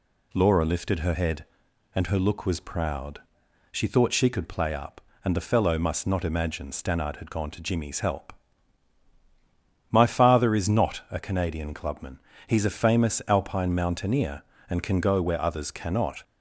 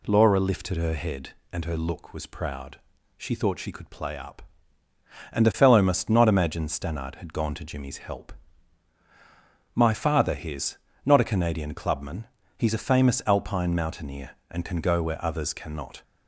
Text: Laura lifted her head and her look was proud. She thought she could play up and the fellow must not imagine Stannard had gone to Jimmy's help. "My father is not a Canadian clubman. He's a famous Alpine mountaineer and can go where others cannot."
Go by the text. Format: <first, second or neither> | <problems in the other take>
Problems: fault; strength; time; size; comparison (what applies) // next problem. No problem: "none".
first | says "his" for "is"; at 10.3 s